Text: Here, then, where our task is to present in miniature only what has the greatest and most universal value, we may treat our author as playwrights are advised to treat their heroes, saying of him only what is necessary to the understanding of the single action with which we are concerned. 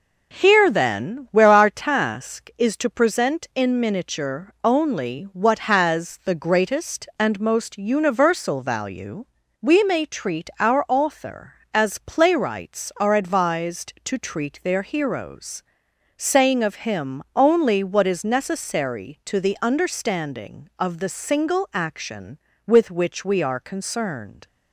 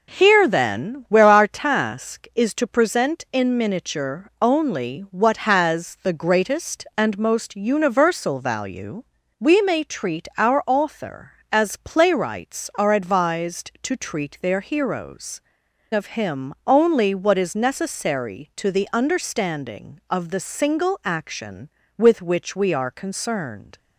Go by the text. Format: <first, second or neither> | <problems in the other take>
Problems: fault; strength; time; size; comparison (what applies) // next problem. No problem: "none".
first | skips "saying"; at 15.6 s